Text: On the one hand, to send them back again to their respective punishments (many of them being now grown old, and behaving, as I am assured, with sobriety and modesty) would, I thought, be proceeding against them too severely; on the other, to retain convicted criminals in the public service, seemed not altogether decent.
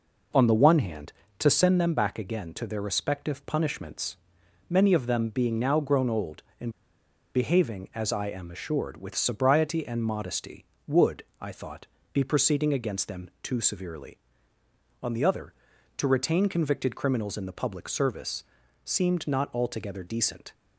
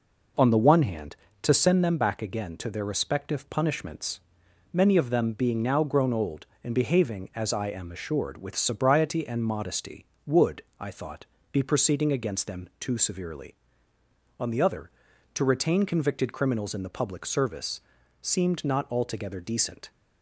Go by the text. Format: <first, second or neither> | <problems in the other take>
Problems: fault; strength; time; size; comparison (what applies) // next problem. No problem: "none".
second | pauses between "and" and "behaving"; noticeable; at 6.7 s; 0.63 s long